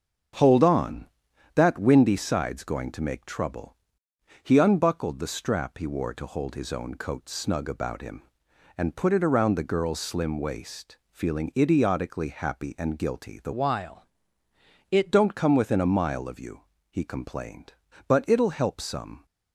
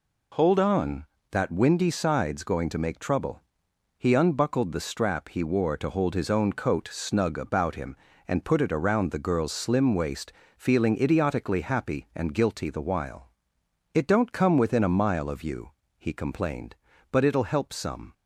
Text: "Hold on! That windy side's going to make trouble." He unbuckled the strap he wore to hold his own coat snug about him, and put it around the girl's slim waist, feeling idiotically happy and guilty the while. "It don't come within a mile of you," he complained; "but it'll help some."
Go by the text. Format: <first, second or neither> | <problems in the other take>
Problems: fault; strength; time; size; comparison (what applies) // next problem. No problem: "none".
second | starts louder than the rest; until 1.8 s; 7 dB // changes voice from "while" to "It"; from 13.5 to 15.1 s; 1.6 s long